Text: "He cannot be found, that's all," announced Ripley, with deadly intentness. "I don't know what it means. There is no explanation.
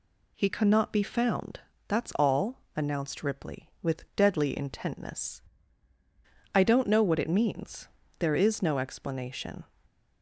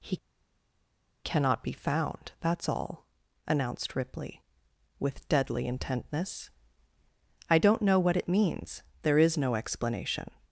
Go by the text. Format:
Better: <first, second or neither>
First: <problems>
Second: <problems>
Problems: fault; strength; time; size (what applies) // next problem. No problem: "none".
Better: first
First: none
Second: pauses between "He" and "cannot"; at 0.1 s; 1.0 s long